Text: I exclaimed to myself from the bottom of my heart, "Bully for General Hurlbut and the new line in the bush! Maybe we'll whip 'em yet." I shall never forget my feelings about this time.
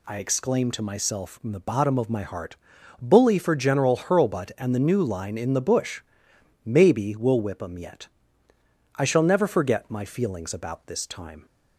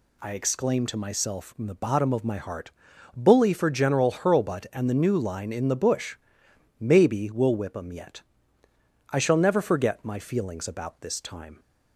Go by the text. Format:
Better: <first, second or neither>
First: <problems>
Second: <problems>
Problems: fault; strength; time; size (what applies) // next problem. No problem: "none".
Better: neither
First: none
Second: none